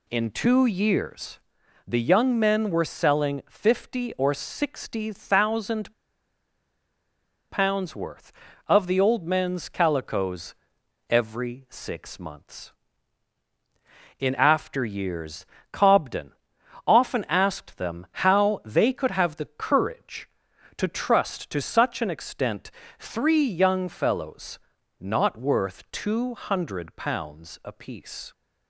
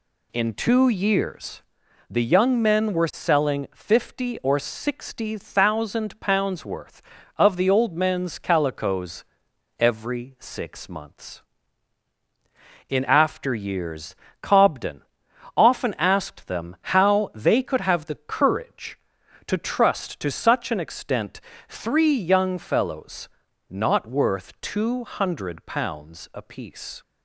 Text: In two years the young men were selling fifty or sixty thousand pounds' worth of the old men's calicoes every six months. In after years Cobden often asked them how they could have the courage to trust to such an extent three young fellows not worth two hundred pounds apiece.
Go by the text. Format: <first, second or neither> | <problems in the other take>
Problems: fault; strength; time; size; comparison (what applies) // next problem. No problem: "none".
second | pauses between "years" and "the"; noticeable; at 1.3 s; 0.46 s long; noticeable in the second // pauses between "thousand" and "pounds"; strong; at 5.9 s; 1.5 s long // pauses between "calicoes" and "every"; noticeable; at 10.5 s; 0.54 s long; noticeable in the second // pauses between "years" and "Cobden"; slight; at 15.4 s; 0.26 s long; slight in the second // pauses between "Cobden" and "often"; noticeable; at 16.3 s; 0.52 s long; noticeable in the second // pauses between "extent" and "three"; slight; at 22.7 s; 0.26 s long; slight in the second // pauses between "fellows" and "not"; at 24.5 s; 0.40 s long; also in the second